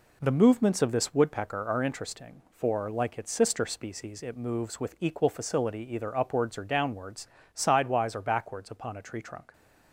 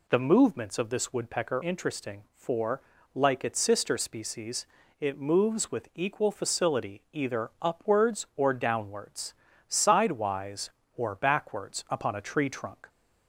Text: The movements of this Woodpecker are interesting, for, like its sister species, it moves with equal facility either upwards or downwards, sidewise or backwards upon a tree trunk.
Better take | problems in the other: first | skips "are"; at 1.6 s

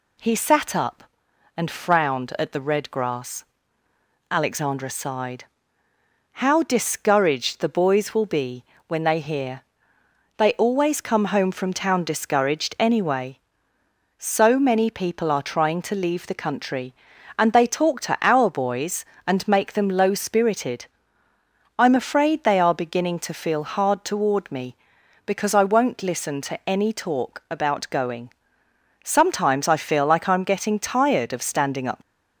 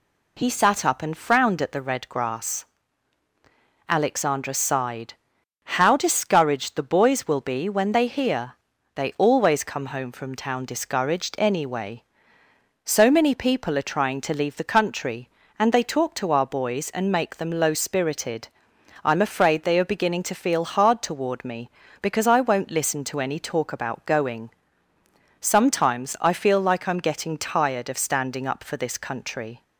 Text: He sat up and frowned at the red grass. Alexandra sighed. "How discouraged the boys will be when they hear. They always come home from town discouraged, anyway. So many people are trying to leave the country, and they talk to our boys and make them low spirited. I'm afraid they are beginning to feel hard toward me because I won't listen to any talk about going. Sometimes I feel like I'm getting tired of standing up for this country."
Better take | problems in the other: second | pauses between "be" and "when"; slight; at 8.6 s; 0.24 s long // stops before "for this country"; at 32.0 s

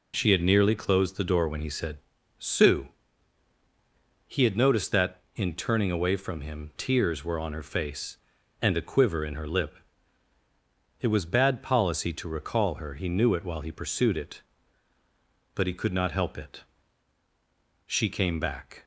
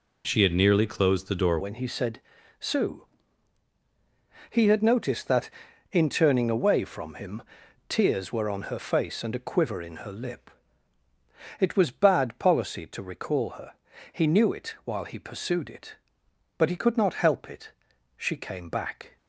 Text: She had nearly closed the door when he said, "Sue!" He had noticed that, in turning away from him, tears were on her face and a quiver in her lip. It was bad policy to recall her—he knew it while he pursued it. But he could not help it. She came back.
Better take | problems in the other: first | changes voice at "when"; from 1.6 s on; 17.5 s long

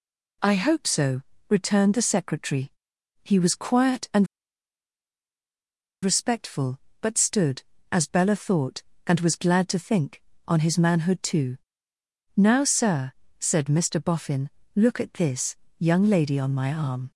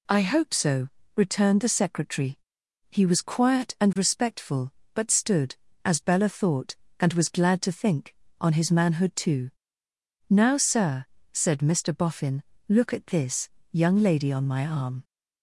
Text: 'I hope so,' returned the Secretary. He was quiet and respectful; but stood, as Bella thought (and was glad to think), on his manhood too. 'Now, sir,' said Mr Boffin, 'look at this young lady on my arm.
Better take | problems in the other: second | pauses between "and" and "respectful"; strong; at 4.2 s; 1.7 s long // pauses between "this" and "young"; slight; at 15.5 s; 0.24 s long; slight in the second

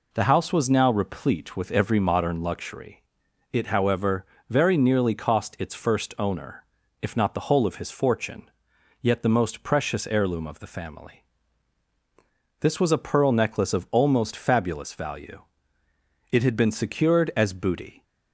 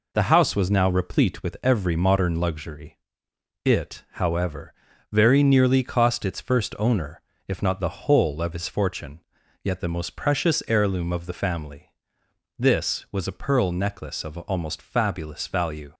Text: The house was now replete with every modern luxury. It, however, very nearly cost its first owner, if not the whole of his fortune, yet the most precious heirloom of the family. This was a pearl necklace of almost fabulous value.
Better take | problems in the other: second | goes on to say "It had been secured as booty"; strong; from 16.3 s on; 1.7 s long

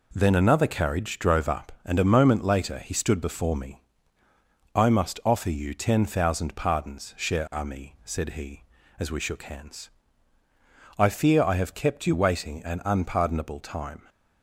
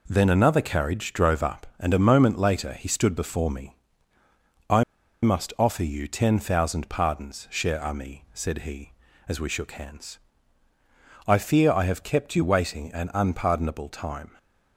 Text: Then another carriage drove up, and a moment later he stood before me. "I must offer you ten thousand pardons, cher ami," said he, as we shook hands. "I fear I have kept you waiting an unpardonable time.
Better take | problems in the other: first | pauses between "I" and "must"; at 4.8 s; 0.39 s long

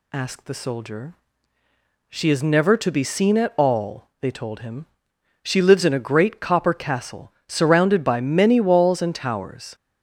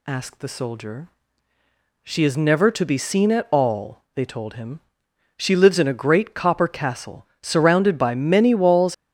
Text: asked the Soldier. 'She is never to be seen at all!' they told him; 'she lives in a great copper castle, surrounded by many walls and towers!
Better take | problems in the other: first | stops before "and towers"; at 8.9 s

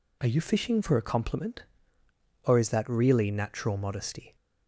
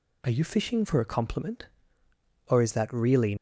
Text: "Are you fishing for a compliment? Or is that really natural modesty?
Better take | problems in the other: first | stops before "natural modesty"; at 3.3 s

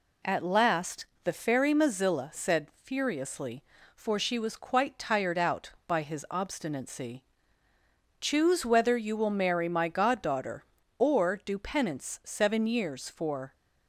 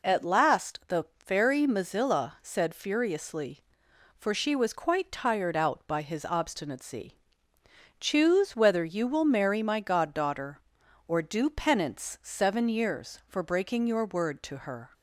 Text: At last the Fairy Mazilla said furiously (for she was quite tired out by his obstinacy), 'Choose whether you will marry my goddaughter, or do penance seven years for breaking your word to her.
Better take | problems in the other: second | pauses between "last" and "the"; slight; at 1.0 s; 0.20 s long // stops before "breaking your word to her"; at 13.5 s

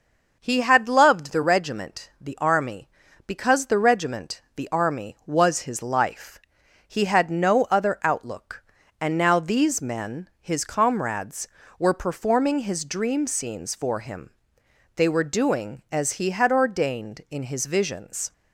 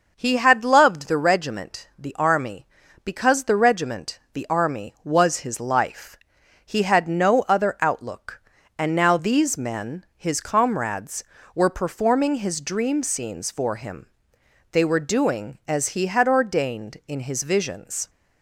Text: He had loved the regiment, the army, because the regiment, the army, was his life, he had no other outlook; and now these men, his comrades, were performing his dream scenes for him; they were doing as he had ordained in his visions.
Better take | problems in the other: neither | none

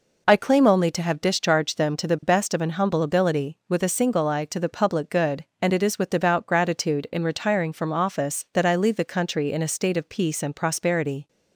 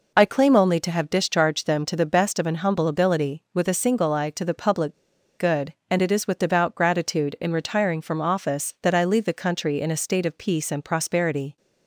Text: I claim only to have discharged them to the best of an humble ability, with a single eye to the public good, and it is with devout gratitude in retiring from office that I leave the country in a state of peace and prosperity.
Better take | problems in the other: first | pauses between "public" and "good"; at 4.9 s; 0.45 s long

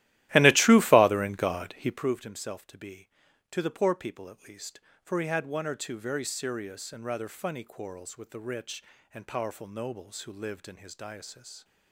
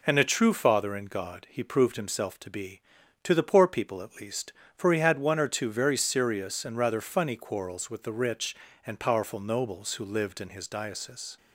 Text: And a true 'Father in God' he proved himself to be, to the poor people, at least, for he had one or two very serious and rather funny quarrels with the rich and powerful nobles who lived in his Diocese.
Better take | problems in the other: second | starts louder than the rest; strong; until 2.1 s; 15 dB

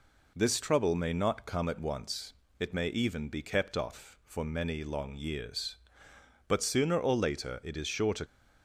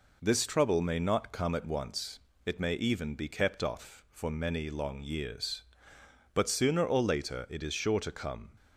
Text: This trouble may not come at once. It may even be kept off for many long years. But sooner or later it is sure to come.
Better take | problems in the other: second | stops before "come"; at 8.2 s

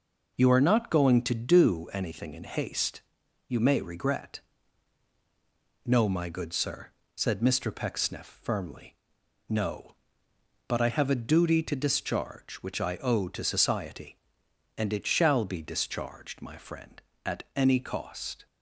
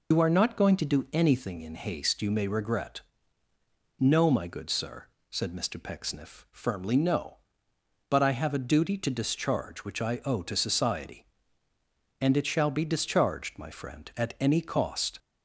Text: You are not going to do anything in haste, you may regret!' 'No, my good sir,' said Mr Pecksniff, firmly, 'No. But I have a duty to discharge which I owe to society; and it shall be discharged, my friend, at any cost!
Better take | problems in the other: first | loses the start of "You"; at 0.1 s; 85 ms

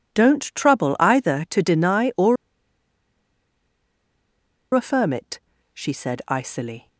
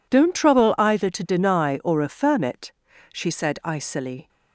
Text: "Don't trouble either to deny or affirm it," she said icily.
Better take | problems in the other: second | pauses between "or" and "affirm"; strong; at 2.3 s; 2.3 s long

